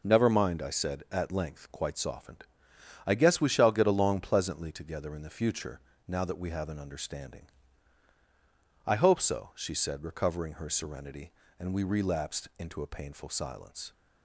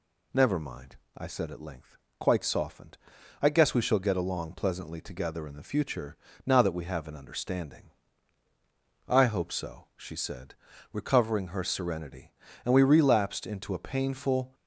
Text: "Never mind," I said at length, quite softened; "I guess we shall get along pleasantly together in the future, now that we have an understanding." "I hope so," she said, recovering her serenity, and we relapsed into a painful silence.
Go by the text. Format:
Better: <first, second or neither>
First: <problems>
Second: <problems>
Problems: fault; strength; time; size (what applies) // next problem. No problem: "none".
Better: first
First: none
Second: stops before "silence"; at 14.5 s